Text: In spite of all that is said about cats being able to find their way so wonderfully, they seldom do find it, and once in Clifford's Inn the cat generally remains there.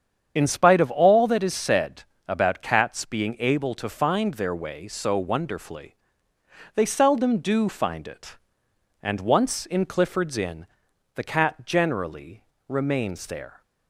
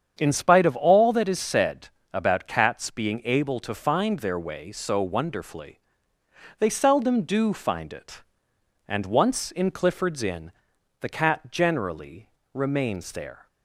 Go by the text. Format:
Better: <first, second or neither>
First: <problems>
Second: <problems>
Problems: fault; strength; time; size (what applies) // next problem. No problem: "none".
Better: second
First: loses the start of "In"; at 0.3 s; 20 ms // starts louder than the rest; strong; until 1.3 s; 8 dB // pauses between "said" and "about"; slight; at 2.0 s; 0.22 s long // pauses between "Inn" and "the"; noticeable; at 10.6 s; 0.50 s long // pauses between "generally" and "remains"; slight; at 12.4 s; 0.24 s long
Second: starts louder than the rest; strong; until 1.1 s; 8 dB // pauses between "said" and "about"; slight; at 1.8 s; 0.22 s long // pauses between "Inn" and "the"; noticeable; at 10.5 s; 0.50 s long // pauses between "generally" and "remains"; slight; at 12.2 s; 0.24 s long